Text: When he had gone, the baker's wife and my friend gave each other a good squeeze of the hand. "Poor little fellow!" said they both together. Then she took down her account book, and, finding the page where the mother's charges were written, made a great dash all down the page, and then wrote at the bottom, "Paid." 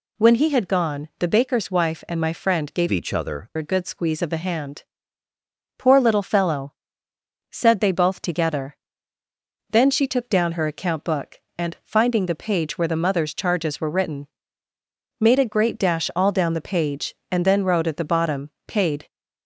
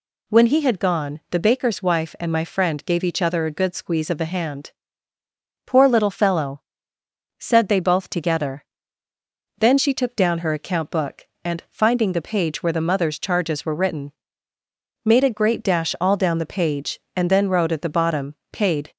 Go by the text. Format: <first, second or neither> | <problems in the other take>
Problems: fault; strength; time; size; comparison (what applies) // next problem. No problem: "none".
second | changes voice from "each" to "other"; from 2.8 to 3.4 s; 0.6 s long